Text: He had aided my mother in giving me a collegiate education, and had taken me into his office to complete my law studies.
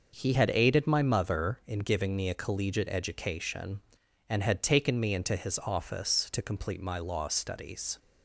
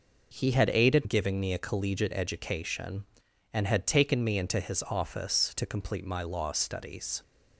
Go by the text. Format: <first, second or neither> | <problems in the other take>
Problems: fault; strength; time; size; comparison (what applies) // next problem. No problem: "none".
first | skips "my mother in"; at 1.0 s